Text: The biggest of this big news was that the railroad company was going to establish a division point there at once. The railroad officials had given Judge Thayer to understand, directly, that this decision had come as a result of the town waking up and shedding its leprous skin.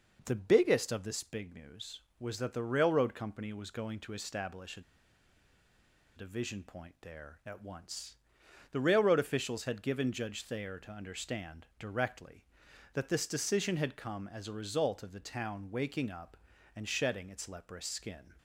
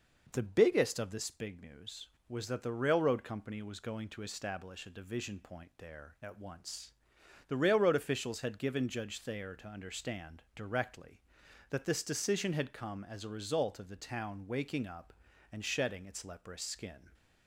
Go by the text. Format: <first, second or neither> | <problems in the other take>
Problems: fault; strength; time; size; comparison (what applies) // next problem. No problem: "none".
second | pauses between "a" and "division"; strong; at 4.8 s; 1.3 s long